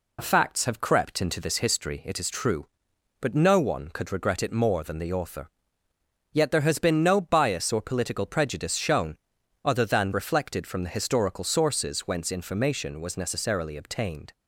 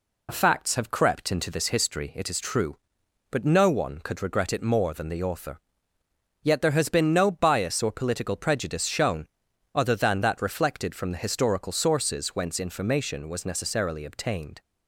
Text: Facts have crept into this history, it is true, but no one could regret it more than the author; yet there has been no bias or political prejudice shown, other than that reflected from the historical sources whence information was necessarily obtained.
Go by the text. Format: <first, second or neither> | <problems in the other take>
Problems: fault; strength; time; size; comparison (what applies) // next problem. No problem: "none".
second | skips "that"; at 10.1 s